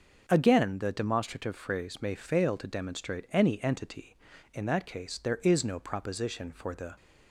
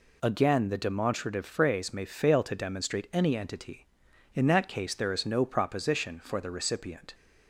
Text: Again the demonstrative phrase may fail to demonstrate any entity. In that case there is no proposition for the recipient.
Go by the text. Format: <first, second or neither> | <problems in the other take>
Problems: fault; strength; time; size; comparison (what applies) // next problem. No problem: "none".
second | starts louder than the rest; noticeable; until 1.3 s; 6 dB // stops before "recipient"; at 6.9 s